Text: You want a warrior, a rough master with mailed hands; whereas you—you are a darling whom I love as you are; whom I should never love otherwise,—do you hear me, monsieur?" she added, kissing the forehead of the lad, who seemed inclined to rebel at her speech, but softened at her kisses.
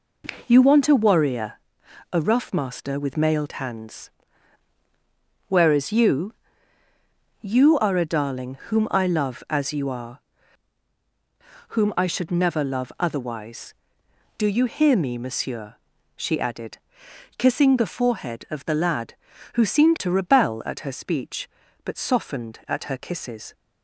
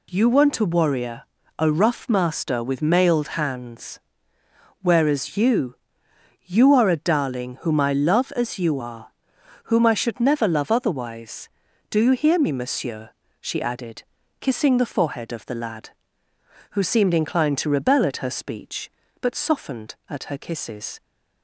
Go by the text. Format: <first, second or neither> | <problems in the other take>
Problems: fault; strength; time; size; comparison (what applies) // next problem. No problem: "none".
second | skips "inclined"; at 19.9 s